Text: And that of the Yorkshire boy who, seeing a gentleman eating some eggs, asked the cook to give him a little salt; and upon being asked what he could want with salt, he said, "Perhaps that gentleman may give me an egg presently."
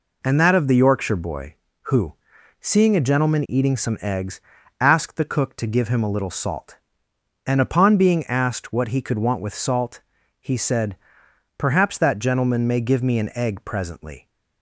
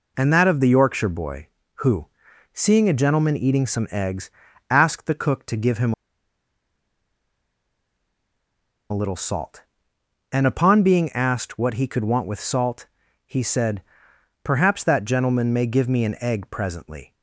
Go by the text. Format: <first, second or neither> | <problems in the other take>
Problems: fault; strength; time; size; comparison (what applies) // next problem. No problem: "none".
first | pauses between "him" and "a"; strong; at 5.9 s; 2.9 s long